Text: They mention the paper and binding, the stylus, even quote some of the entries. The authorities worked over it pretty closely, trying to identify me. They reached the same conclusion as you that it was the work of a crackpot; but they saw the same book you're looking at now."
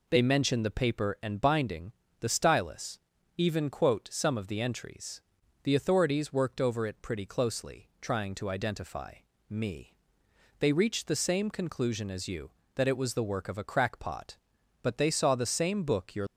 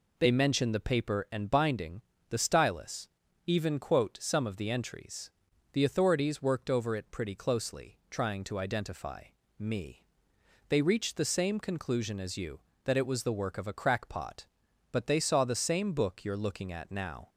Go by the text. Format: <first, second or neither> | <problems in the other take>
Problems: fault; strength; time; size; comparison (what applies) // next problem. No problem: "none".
second | pauses between "identify" and "me"; at 9.1 s; 0.38 s long; also in the second // stops before "looking at now"; at 16.2 s